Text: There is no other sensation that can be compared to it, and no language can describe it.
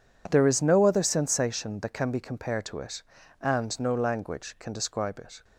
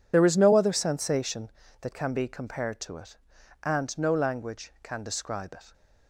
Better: first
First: none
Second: loses the start of "There"; at 0.1 s; 35 ms

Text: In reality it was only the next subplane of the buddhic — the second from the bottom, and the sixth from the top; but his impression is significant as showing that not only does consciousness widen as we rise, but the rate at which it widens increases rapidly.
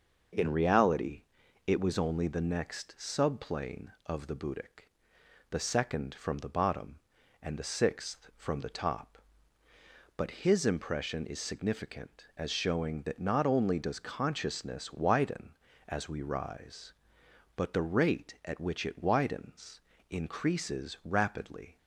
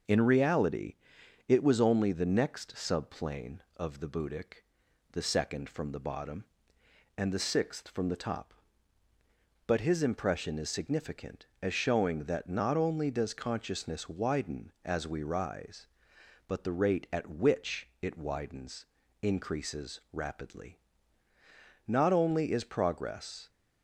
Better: first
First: starts louder than the rest; noticeable; until 1.8 s; 6 dB // pauses between "reality" and "it"; noticeable; at 1.2 s; 0.46 s long // pauses between "widens" and "increases"; slight; at 19.8 s; 0.28 s long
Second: starts louder than the rest; until 1.6 s; 6 dB // pauses between "reality" and "it"; noticeable; at 0.9 s; 0.52 s long // pauses between "widens" and "increases"; slight; at 18.8 s; 0.36 s long // goes on to say "Not only is progress"; from 21.8 s on; 1.6 s long

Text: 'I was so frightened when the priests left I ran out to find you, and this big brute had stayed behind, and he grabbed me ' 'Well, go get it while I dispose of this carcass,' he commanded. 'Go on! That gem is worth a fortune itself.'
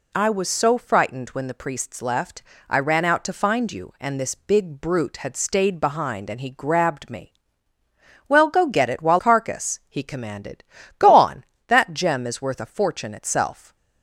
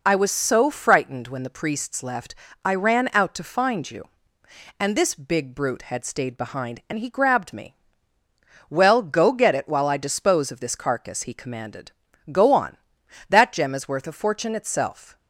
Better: second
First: pauses between "left" and "I"; slight; at 2.4 s; 0.26 s long // skips "I dispose of this"; at 9.1 s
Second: pauses between "left" and "I"; slight; at 2.3 s; 0.30 s long

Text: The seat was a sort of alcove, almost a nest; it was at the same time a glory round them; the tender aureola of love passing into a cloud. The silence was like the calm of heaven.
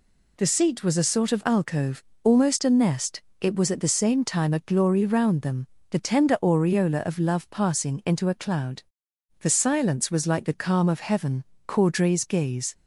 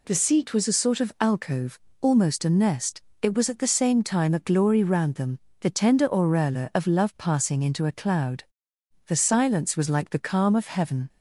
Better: second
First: goes on to say "Caudray's gaze"; noticeable; from 11.6 s on; 1.0 s long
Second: none

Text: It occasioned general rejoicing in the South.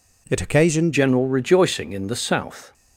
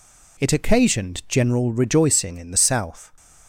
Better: second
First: changes voice at "general"; from 0.9 s on; 1.8 s long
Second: none

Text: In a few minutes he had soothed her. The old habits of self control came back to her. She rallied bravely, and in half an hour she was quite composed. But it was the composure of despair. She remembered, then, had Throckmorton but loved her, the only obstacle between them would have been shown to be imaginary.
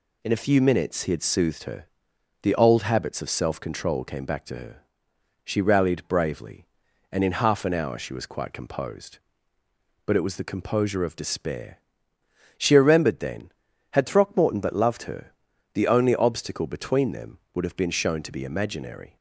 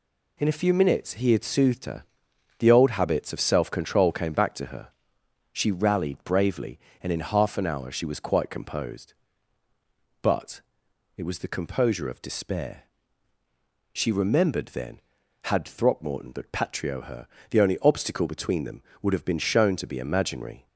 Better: first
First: none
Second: pauses between "But" and "it"; noticeable; at 10.6 s; 0.54 s long // says "patrio" for "loved"; at 16.5 s

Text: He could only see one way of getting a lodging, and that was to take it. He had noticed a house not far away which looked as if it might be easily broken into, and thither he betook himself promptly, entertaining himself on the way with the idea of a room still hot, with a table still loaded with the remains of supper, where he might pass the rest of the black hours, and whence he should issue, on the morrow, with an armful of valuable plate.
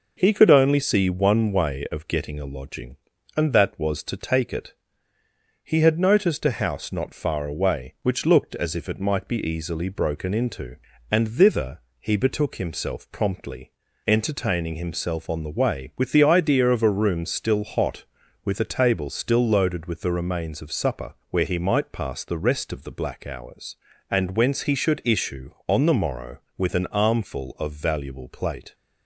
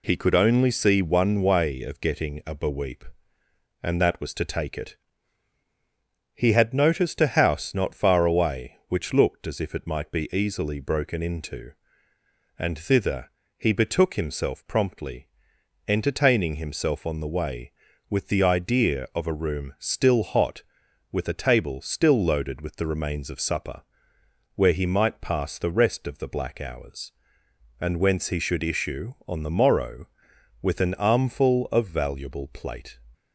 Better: first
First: pauses between "thither" and "he"; slight; at 11.7 s; 0.22 s long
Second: says "beweep" for "lodging"; at 2.5 s // pauses between "thither" and "he"; slight; at 13.3 s; 0.26 s long

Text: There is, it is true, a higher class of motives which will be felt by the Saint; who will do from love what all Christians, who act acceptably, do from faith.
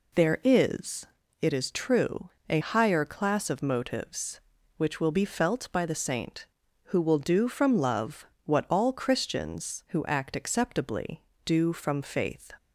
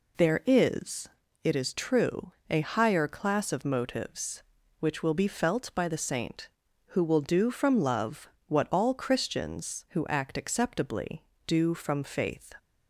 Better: neither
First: pauses between "love" and "what"; slight; at 8.2 s; 0.18 s long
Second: pauses between "love" and "what"; slight; at 8.2 s; 0.18 s long

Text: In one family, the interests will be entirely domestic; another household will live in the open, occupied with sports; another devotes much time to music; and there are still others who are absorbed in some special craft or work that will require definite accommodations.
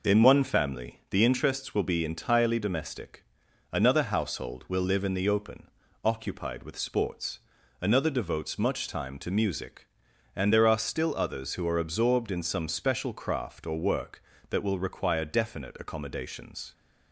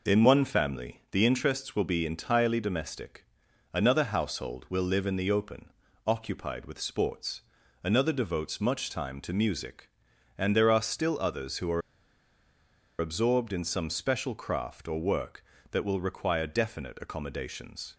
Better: first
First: none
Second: pauses between "are" and "absorbed"; at 11.8 s; 1.1 s long

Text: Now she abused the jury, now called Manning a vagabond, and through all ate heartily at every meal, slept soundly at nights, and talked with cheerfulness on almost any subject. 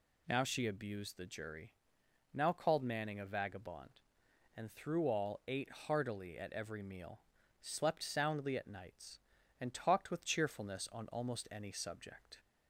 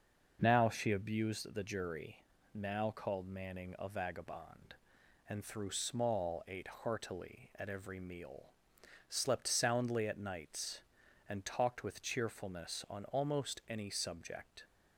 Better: first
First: none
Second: says "small" for "all"; at 5.7 s

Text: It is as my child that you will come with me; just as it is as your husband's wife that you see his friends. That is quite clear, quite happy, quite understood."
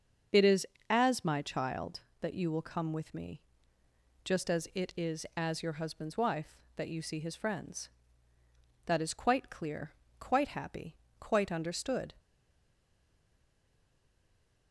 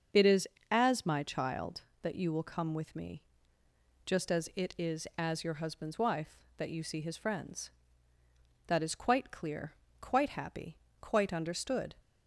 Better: second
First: starts louder than the rest; until 1.5 s; 6 dB // stays silent after the last word; from 12.1 s on; 2.6 s long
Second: starts louder than the rest; until 1.3 s; 6 dB

